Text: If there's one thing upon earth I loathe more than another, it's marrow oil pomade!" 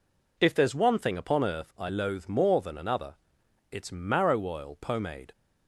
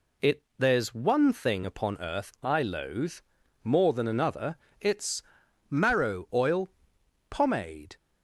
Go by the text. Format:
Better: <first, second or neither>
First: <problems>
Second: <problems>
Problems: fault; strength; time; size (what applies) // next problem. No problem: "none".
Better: first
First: none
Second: says "It" for "If"; at 0.2 s // pauses between "loathe" and "more"; noticeable; at 3.1 s; 0.50 s long // pauses between "it's" and "marrow"; noticeable; at 5.2 s; 0.48 s long // pauses between "oil" and "pomade"; noticeable; at 6.7 s; 0.58 s long